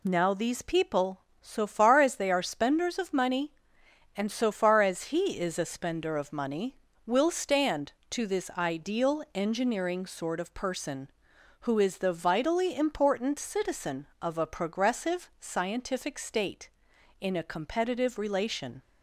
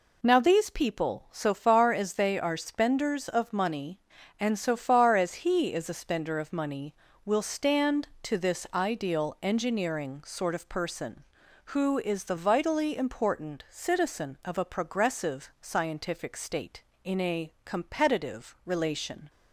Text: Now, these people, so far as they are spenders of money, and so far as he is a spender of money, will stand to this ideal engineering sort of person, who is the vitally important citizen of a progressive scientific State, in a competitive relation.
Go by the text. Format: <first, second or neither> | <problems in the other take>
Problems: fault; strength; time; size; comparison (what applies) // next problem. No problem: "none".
neither | none